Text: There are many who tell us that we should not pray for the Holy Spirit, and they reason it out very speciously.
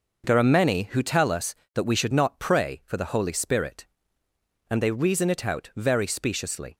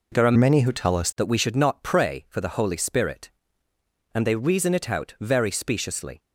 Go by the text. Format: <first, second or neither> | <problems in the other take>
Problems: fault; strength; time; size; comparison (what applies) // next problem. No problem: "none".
first | changes voice from "many" to "us"; from 0.3 to 1.0 s; 0.7 s long